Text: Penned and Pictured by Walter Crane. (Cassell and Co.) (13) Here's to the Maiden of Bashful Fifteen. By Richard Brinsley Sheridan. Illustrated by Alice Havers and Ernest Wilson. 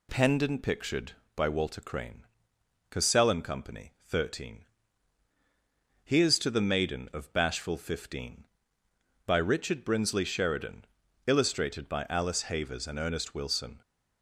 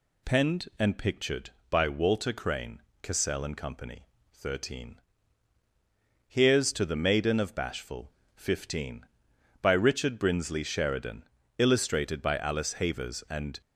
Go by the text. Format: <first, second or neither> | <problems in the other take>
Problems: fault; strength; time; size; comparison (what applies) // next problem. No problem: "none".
first | pauses between "Bashful" and "Fifteen"; slight; at 8.1 s; 0.24 s long // stops before "Ernest Wilson"; at 13.6 s